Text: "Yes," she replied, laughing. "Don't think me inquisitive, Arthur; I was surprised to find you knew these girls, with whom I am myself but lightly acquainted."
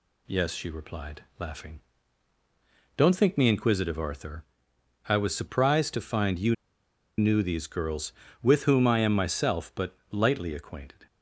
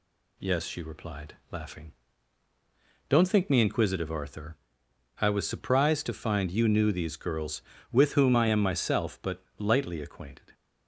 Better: second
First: pauses between "you" and "knew"; noticeable; at 6.5 s; 0.63 s long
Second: none

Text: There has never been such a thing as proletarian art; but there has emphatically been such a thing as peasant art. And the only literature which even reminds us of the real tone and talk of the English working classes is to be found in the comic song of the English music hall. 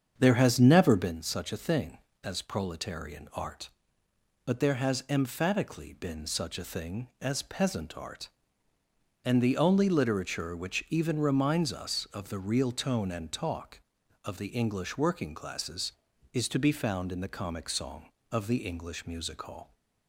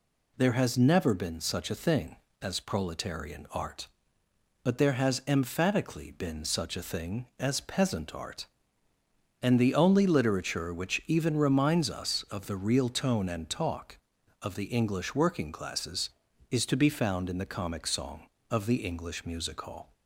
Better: second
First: starts louder than the rest; strong; until 1.2 s; 7.5 dB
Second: none

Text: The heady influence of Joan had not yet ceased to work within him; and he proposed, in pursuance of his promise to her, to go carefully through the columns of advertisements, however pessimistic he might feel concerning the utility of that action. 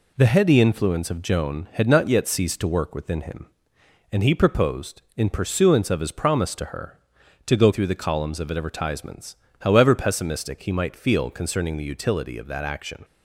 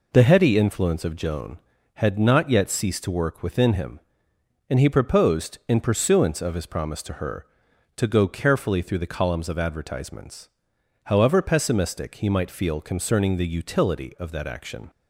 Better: second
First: skips "carefully"; at 7.7 s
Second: none

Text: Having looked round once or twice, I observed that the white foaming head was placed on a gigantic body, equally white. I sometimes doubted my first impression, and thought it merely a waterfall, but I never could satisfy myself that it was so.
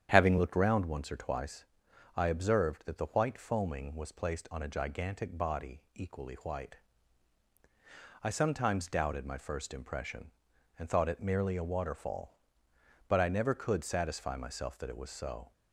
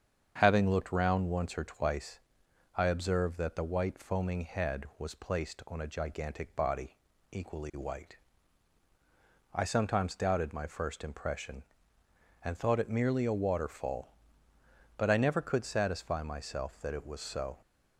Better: second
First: starts louder than the rest; strong; until 1.1 s; 9.5 dB // skips "head"; at 3.9 s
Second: starts louder than the rest; strong; until 1.4 s; 7.5 dB

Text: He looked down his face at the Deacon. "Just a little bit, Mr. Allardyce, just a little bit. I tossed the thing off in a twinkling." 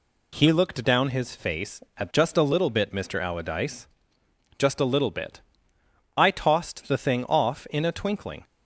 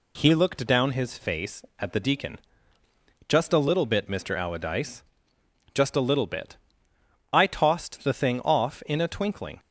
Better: second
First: skips "the Deacon"; at 2.1 s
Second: none

